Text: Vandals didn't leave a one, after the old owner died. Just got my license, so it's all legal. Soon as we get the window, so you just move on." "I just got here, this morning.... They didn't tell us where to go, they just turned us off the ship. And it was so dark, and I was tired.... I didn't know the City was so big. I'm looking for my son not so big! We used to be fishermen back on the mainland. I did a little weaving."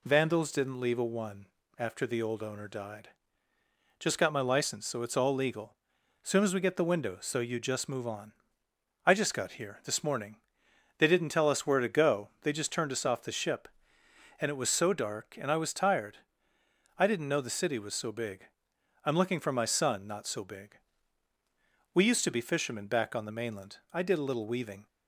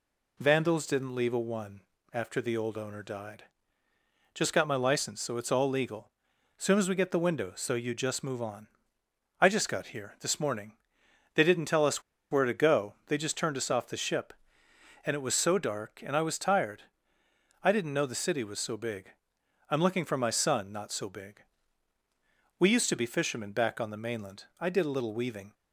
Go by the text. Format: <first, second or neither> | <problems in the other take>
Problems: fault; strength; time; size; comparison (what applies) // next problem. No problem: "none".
first | pauses between "us" and "where"; slight; at 12.0 s; 0.29 s long